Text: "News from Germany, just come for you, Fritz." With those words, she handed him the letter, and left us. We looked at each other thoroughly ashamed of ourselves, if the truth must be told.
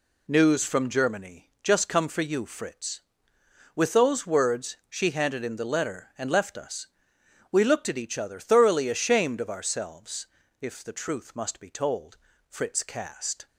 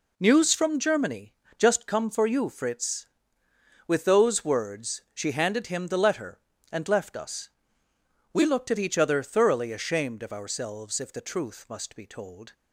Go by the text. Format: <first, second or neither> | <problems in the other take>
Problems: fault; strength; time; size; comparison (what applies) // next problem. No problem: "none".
second | goes on to say "Fritz cast"; noticeable; from 12.4 s on; 1.0 s long